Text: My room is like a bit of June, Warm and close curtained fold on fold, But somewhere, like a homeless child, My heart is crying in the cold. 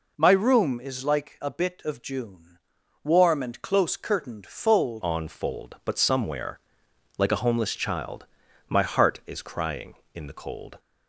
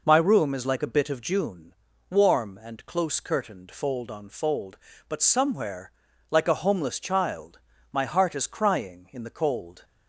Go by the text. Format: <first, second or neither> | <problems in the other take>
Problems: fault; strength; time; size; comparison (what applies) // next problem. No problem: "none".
second | changes voice at "on"; from 5.0 s on; 5.7 s long